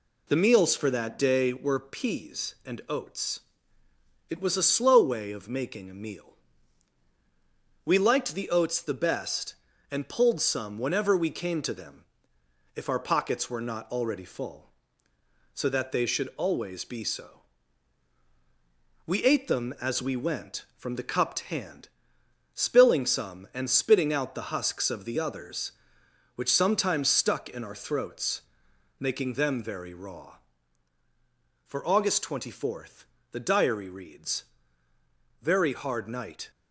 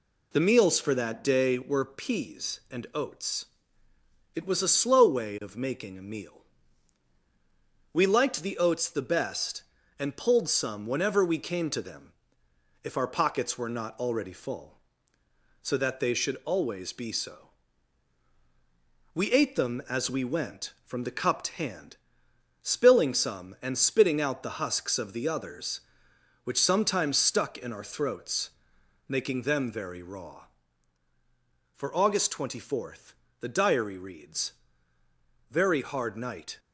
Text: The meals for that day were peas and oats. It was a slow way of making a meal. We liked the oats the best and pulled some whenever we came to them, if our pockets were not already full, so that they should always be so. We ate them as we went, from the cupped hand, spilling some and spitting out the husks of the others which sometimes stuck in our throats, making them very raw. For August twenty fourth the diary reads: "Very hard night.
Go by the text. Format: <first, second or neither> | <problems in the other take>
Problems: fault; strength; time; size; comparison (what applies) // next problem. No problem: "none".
neither | pauses between "fourth" and "the"; slight; the same in both